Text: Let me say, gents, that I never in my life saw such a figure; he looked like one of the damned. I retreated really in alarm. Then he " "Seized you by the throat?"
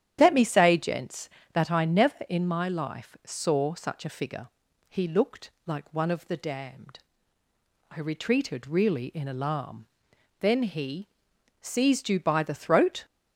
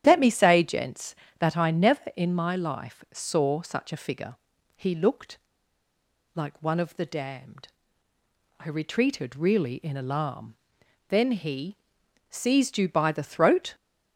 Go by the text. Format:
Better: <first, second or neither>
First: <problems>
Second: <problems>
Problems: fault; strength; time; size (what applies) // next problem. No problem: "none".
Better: first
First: starts louder than the rest; strong; until 1.2 s; 10 dB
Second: starts louder than the rest; strong; until 1.0 s; 10 dB // pauses between "looked" and "like"; noticeable; at 5.3 s; 0.93 s long